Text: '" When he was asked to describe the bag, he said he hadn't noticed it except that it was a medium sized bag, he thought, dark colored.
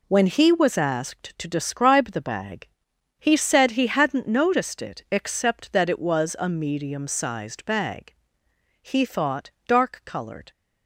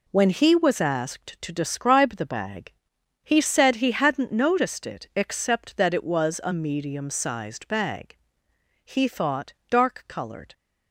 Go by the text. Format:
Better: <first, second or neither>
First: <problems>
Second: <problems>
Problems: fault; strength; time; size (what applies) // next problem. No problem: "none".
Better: neither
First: none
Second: none